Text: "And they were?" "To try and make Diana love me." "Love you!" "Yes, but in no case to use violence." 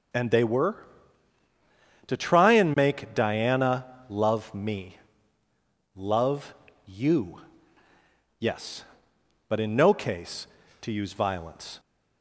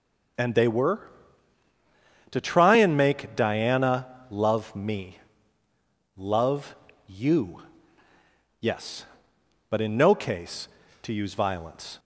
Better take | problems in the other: neither | pauses between "Diana" and "love"; slight; the same in both // pauses between "Love" and "you"; slight; the same in both

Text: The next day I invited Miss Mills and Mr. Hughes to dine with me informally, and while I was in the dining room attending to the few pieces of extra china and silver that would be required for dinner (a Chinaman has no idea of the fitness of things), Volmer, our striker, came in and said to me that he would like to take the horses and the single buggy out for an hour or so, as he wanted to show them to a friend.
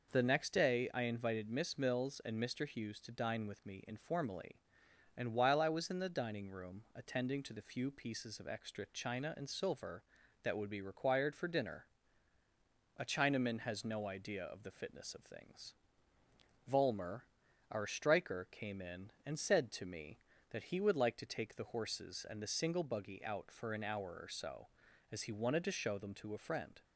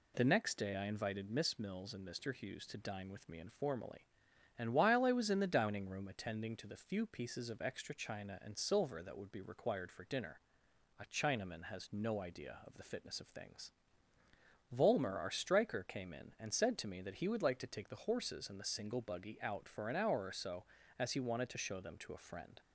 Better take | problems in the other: neither | none

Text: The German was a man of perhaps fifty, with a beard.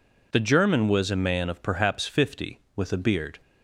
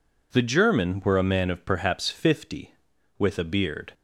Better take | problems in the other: first | says "were" for "was"; at 1.0 s

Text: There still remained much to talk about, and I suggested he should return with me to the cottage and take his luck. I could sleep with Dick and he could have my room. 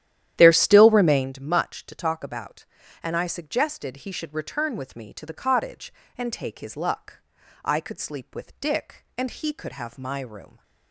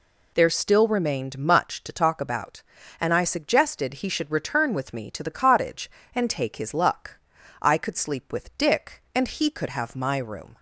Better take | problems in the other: second | starts louder than the rest; strong; until 1.3 s; 11.5 dB

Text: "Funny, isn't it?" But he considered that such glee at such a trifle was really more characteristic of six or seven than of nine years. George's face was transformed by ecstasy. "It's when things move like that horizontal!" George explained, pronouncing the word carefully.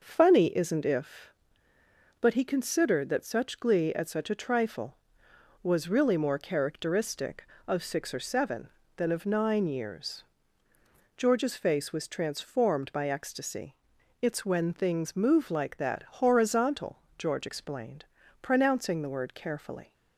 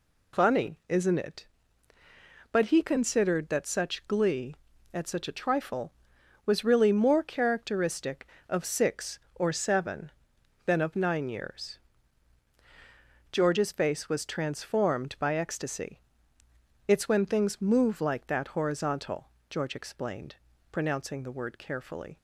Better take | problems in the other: second | says "if" for "it"; at 0.8 s

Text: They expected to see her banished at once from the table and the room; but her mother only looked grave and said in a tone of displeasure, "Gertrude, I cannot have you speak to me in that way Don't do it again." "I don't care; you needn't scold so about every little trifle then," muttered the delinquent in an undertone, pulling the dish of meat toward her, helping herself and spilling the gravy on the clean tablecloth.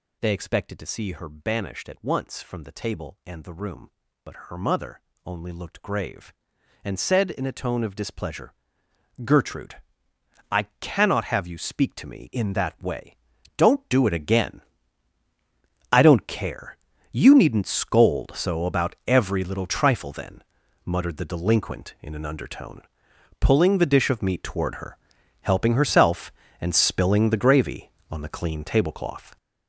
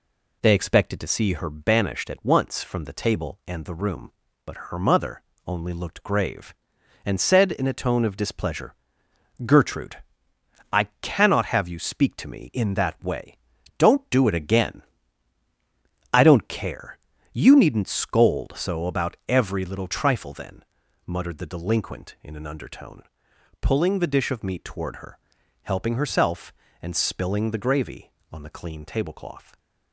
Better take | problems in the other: second | gets louder; strong; throughout; 9 dB // pauses between "mother" and "only"; slight; at 5.0 s; 0.26 s long; slight in the second // pauses between "I" and "cannot"; slight; at 10.6 s; 0.18 s long; slight in the second // pauses between "way" and "Don't"; at 13.1 s; 0.42 s long; also in the second

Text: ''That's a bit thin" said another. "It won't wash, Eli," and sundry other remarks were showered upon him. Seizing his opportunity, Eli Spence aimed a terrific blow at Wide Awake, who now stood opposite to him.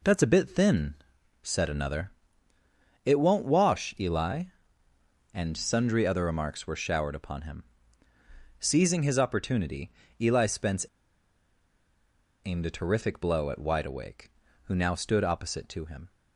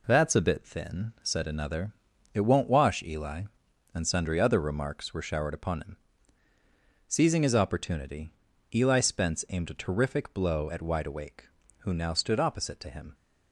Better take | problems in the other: second | pauses between "thin" and "said"; noticeable; at 0.9 s; 0.48 s long // pauses between "Spence" and "aimed"; strong; at 10.8 s; 1.6 s long

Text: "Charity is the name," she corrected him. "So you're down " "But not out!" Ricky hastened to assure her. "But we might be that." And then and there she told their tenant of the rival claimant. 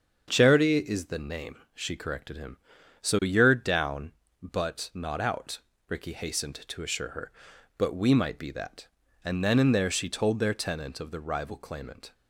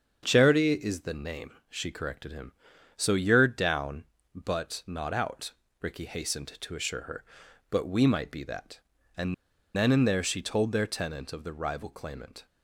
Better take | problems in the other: first | starts louder than the rest; until 1.2 s; 7 dB; also in the first // pauses between "And" and "then"; at 9.3 s; 0.41 s long

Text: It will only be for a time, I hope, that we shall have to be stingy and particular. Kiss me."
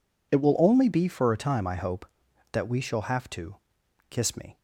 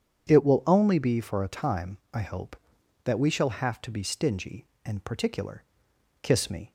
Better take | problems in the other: second | skips "be stingy and particular"; at 3.8 s

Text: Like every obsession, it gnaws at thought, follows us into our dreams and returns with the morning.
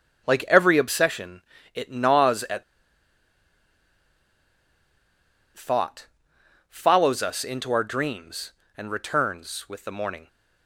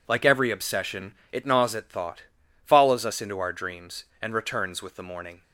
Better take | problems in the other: second | starts louder than the rest; strong; until 1.2 s; 8.5 dB // pauses between "at" and "thought"; strong; at 2.6 s; 2.9 s long

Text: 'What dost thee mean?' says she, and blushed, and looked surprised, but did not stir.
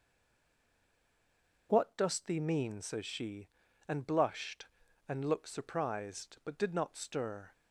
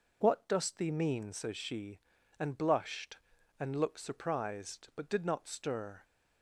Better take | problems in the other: second | stays silent before the first word; noticeable; until 1.6 s; 1.6 s long

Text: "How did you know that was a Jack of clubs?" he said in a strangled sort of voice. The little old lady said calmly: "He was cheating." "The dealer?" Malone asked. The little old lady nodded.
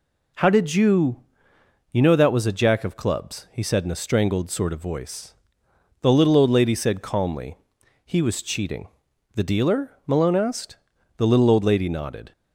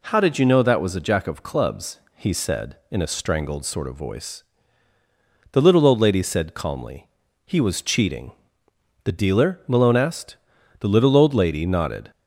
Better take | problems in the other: second | says "you" twice; at 1.9 s

